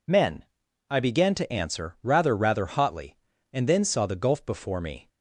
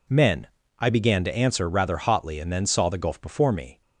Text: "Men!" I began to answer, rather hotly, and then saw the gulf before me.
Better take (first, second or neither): second